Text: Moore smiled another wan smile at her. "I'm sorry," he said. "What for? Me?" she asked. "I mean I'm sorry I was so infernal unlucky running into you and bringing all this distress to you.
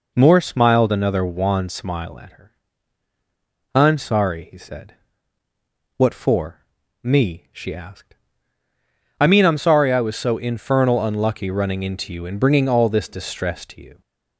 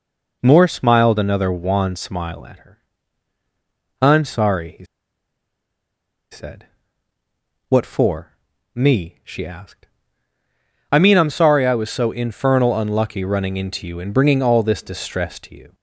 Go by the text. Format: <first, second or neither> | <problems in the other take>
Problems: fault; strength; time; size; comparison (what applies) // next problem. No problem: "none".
first | pauses between "he" and "said"; strong; at 4.8 s; 1.4 s long